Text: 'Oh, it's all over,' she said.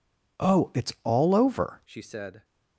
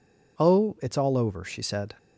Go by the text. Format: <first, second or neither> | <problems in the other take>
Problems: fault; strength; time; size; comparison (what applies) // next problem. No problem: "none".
second | changes voice at "she"; from 1.8 s on; 0.6 s long